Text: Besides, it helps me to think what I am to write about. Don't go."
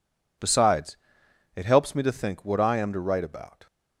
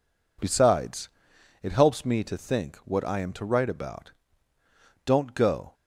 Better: second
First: stops before "Don't go"; at 3.6 s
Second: none

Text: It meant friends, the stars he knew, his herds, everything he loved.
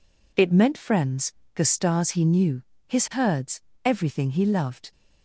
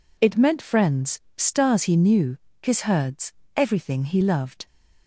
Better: first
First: none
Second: skips "the"; at 1.2 s

